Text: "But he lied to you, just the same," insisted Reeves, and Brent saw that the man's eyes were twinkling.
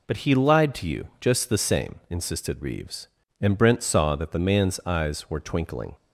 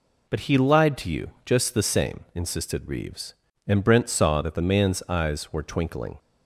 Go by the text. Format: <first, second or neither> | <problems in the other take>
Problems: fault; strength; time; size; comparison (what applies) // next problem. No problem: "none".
neither | none